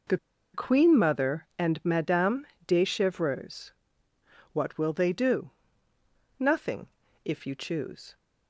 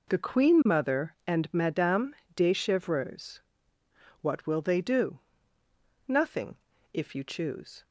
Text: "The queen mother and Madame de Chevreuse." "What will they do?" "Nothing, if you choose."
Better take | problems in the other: second | pauses between "The" and "queen"; at 0.1 s; 0.37 s long // pauses between "Madame" and "de"; slight; at 2.4 s; 0.22 s long; slight in the second

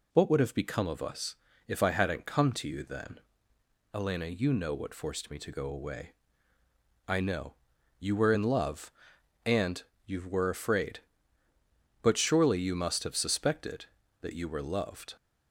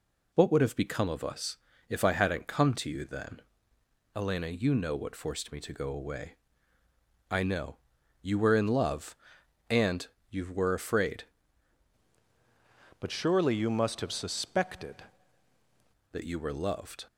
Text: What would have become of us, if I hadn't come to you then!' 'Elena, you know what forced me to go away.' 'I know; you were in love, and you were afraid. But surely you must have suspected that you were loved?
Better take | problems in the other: first | pauses between "and" and "you"; slight; at 10.0 s; 0.24 s long; slight in the first // changes voice from "But" to "suspected"; from 12.9 to 15.0 s; 2.1 s long

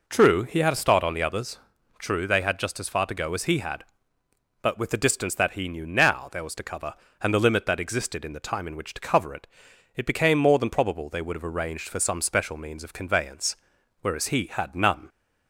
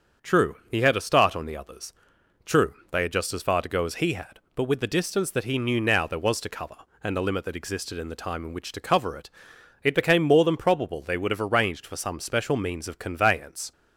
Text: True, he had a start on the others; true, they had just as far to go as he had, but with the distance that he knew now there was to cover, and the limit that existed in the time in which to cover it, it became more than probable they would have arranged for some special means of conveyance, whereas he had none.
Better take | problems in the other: first | starts louder than the rest; until 1.3 s; 6.5 dB // stops before "whereas he had none"; at 13.7 s

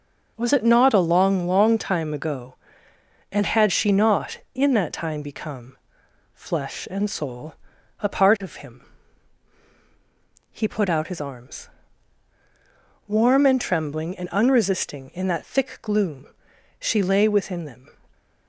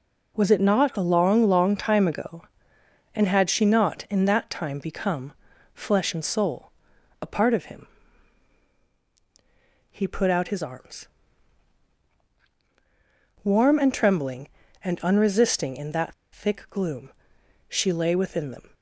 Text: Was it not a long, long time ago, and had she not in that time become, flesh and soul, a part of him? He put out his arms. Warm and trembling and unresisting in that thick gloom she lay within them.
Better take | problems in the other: first | pauses between "that" and "thick"; slight; at 16.1 s; 0.19 s long // pauses between "gloom" and "she"; noticeable; at 17.1 s; 0.56 s long; noticeable in the first

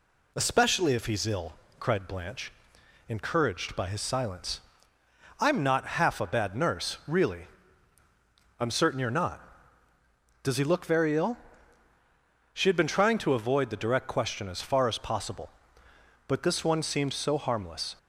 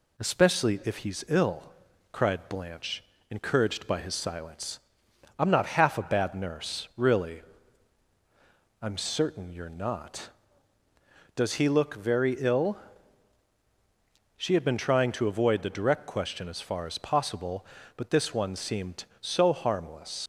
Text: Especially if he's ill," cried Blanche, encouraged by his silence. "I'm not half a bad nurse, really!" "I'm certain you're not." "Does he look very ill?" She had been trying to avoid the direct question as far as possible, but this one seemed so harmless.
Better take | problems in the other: first | leaves "harmless" unfinished; at 20.2 s; 70 ms

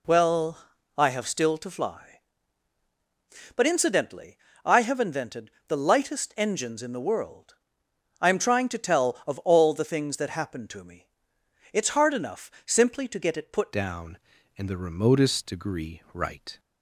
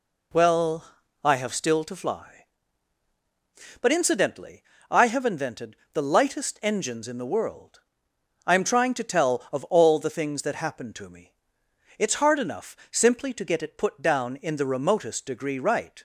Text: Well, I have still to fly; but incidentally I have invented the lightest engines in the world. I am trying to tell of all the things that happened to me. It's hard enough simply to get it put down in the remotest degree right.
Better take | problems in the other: second | pauses between "incidentally" and "I"; slight; at 4.3 s; 0.26 s long; slight in the second // pauses between "invented" and "the"; slight; at 5.4 s; 0.18 s long; slight in the second // changes voice at "down"; from 13.7 s on; 2.8 s long

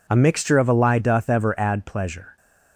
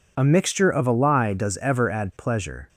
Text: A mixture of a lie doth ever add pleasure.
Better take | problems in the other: first | says "does" for "doth"; at 1.3 s

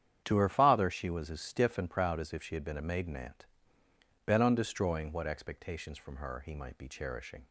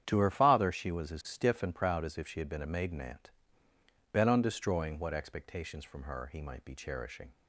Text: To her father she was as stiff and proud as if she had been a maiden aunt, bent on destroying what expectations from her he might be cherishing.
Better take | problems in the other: neither | starts louder than the rest; strong; the same in both

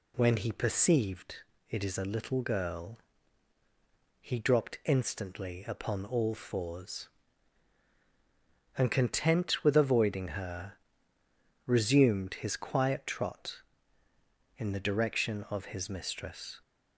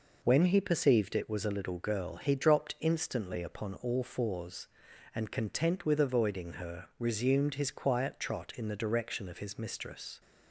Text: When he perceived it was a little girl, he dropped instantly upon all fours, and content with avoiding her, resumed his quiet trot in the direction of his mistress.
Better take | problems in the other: second | pauses between "perceived" and "it"; slight; at 1.4 s; 0.28 s long // says "is" for "was"; at 1.8 s

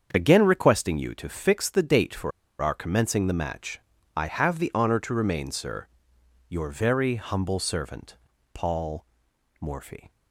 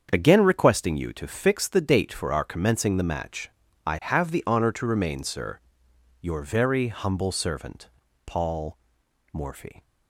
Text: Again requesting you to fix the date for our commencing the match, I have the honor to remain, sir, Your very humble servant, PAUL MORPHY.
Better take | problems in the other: second | starts louder than the rest; strong; until 1.1 s; 7.5 dB; strong in the second // pauses between "for" and "our"; slight; at 2.3 s; 0.30 s long // pauses between "PAUL" and "MORPHY"; noticeable; at 9.0 s; 0.56 s long; noticeable in the second

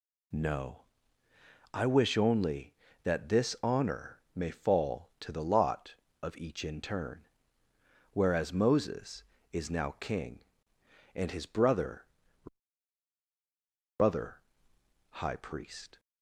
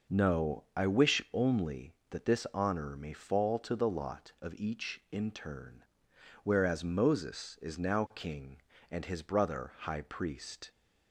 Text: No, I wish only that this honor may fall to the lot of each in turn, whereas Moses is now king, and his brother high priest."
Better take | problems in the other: second | says "brother" twice; at 13.9 s

